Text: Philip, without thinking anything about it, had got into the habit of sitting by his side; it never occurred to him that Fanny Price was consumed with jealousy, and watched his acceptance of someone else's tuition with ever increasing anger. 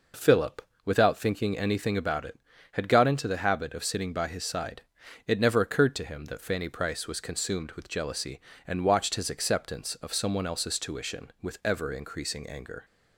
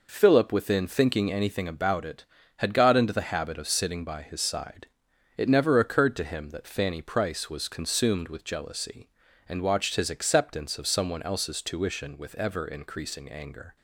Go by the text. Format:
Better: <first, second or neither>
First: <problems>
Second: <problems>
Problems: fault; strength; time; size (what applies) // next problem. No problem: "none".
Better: first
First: none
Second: says "within" for "without"; at 0.5 s